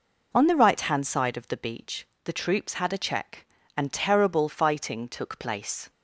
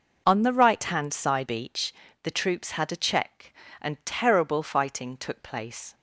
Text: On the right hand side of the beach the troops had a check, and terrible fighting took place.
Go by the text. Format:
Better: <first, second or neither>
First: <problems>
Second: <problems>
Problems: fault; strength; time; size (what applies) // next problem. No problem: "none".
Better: first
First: pauses between "beach" and "the"; slight; at 2.0 s; 0.16 s long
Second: skips "of the"; at 1.4 s // pauses between "beach" and "the"; slight; at 1.9 s; 0.30 s long